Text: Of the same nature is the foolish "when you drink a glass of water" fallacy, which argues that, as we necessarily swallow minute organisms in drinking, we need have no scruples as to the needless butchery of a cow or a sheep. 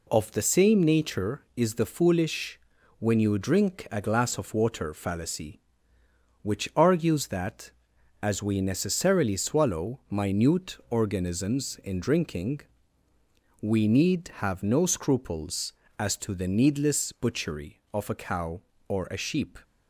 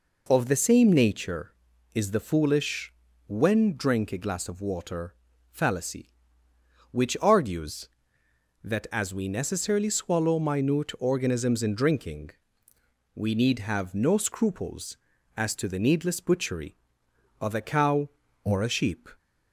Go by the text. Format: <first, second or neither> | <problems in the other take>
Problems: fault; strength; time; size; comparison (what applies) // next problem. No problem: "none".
first | pauses between "foolish" and "when"; at 2.9 s; 0.38 s long; also in the first // skips "you"; at 3.7 s // pauses between "water" and "fallacy"; at 5.1 s; 0.38 s long